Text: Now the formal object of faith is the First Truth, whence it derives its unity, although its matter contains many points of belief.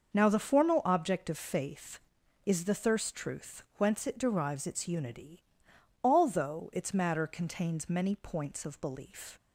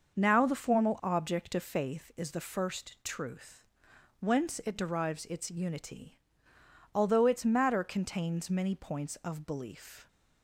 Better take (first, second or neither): second